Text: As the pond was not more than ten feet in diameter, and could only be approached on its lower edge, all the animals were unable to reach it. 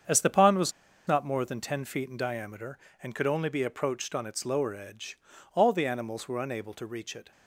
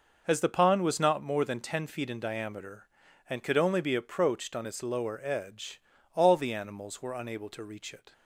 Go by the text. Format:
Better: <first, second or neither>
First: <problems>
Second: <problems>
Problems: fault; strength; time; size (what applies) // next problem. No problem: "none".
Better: second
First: starts louder than the rest; strong; until 1.4 s; 7.5 dB // pauses between "was" and "not"; slight; at 0.7 s; 0.35 s long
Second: none